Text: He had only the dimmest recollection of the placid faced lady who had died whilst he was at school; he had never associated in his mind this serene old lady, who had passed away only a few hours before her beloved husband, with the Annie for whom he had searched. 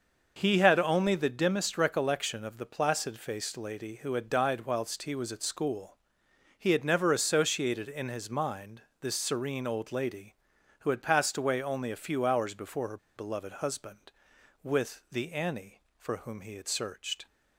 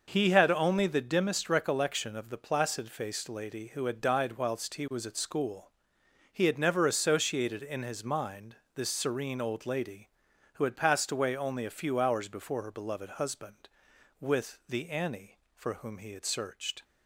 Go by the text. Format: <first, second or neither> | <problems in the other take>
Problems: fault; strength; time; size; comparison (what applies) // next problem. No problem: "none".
second | starts louder than the rest; noticeable; until 1.3 s; 6 dB // pauses between "mind" and "this"; slight; at 8.8 s; 0.18 s long; slight in the second // pauses between "her" and "beloved"; slight; at 12.9 s; 0.19 s long